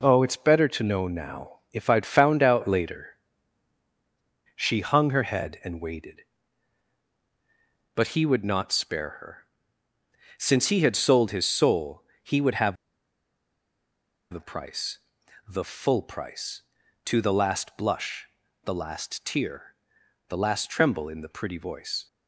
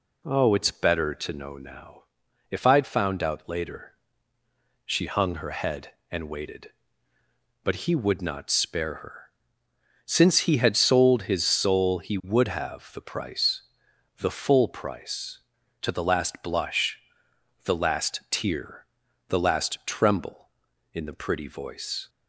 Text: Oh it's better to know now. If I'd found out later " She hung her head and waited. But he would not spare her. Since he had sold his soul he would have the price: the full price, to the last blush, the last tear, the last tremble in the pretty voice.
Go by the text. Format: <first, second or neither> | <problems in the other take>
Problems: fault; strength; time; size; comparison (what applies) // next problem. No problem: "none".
second | pauses between "soul" and "he"; slight; at 12.0 s; 0.22 s long // pauses between "have" and "the"; strong; at 12.7 s; 1.5 s long